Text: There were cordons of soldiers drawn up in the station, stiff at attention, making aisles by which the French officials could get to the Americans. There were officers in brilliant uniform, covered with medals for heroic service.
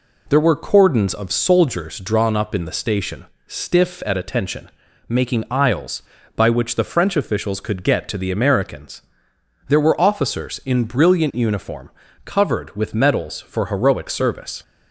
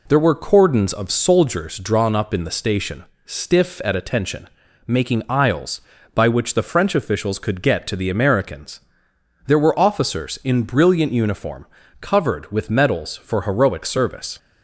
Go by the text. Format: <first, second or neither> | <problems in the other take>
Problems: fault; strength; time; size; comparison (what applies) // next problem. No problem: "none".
neither | none